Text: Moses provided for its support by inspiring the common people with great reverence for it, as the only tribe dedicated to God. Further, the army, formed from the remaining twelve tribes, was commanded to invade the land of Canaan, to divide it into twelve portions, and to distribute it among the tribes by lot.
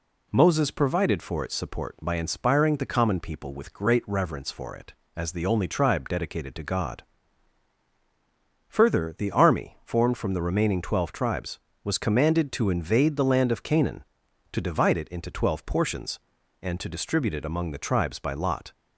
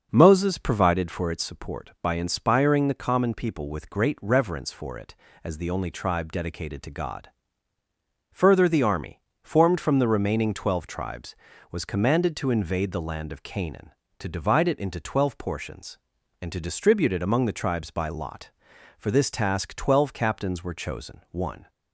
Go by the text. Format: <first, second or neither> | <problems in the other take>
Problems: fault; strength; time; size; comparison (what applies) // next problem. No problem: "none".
first | starts louder than the rest; until 1.1 s; 6.5 dB // goes on to say "For this task twelve captains were chosen one"; strong; from 18.9 s on; 2.7 s long